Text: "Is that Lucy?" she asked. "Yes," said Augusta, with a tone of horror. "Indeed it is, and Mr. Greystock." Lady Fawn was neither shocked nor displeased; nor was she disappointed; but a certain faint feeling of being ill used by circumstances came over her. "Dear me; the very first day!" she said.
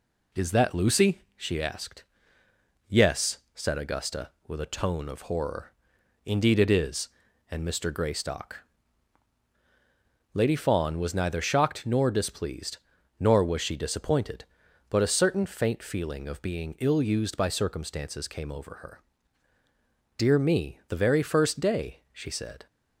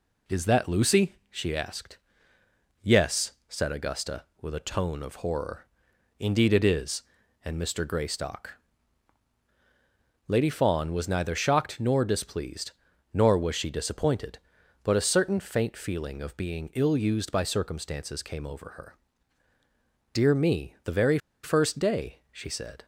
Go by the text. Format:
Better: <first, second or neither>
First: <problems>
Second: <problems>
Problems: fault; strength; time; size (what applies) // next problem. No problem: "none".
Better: first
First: none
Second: pauses between "very" and "first"; slight; at 21.1 s; 0.25 s long